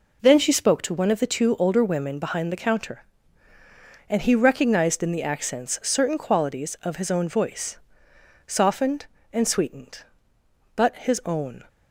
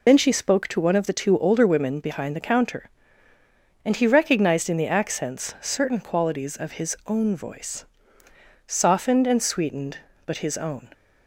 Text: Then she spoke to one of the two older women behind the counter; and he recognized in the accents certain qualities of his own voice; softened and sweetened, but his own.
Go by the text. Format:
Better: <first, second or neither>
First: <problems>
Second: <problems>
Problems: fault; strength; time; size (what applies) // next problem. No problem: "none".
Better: first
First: none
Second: loses the start of "Then"; at 0.0 s; 70 ms